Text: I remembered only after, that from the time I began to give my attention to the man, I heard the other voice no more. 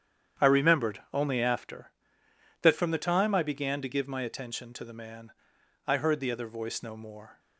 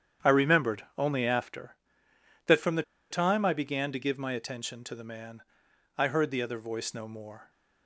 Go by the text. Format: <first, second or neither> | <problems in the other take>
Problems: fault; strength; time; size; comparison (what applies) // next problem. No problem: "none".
first | starts louder than the rest; strong; until 1.3 s; 9 dB; strong in the first // pauses between "the" and "time"; slight; at 2.8 s; 0.28 s long